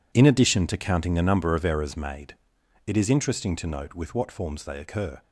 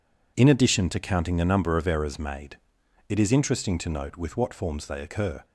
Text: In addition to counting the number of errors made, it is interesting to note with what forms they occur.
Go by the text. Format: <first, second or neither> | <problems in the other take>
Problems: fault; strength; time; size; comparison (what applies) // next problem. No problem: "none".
second | gets quieter; strong; throughout; 13 dB